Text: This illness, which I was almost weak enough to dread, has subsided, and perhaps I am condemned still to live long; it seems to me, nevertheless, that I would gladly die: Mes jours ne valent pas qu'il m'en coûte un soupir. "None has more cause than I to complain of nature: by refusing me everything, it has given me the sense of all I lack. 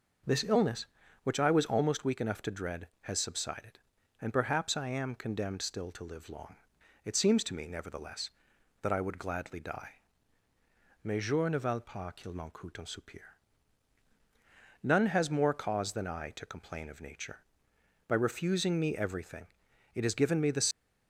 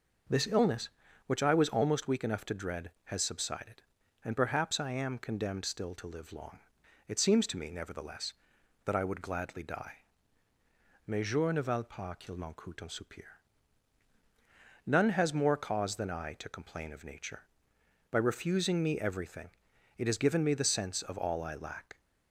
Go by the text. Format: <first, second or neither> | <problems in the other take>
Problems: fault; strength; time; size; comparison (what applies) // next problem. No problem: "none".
second | stops before "sense of all I lack"; at 20.7 s